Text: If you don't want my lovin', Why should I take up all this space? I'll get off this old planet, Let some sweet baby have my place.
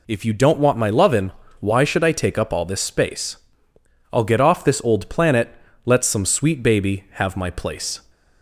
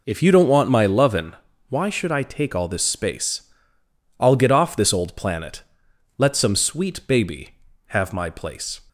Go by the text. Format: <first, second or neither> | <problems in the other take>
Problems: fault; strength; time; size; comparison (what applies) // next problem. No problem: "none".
first | skips "up"; at 2.5 s